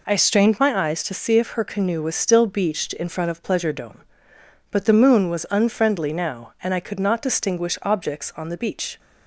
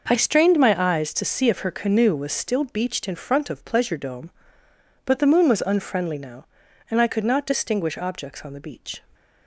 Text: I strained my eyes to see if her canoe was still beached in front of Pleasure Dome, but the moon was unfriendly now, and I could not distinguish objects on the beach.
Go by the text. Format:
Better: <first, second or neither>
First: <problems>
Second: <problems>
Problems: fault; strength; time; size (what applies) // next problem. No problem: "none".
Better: neither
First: none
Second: none